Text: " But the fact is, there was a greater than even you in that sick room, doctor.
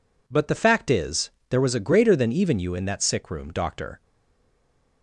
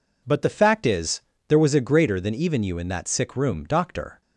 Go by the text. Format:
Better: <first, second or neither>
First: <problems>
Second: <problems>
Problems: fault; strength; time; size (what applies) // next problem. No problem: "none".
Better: second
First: stays silent after the last word; from 4.0 s on; 1.0 s long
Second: none